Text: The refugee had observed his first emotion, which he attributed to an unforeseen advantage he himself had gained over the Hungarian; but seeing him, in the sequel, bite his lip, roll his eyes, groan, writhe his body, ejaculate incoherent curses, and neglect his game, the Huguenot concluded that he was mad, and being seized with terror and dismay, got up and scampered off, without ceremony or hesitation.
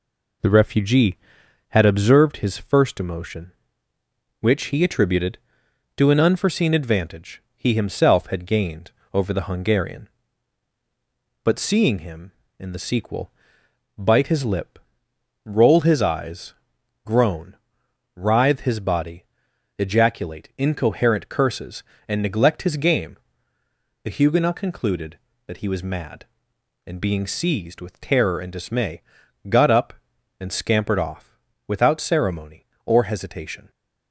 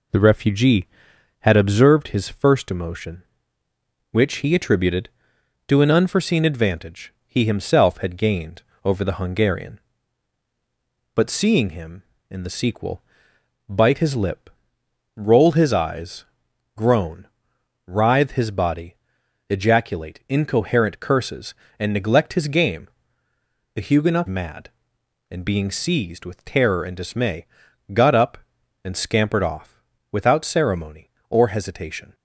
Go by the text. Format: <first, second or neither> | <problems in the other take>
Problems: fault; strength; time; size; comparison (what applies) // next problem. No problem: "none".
first | pauses between "gained" and "over"; slight; at 8.6 s; 0.20 s long; slight in the first // skips "concluded that he was"; at 24.2 s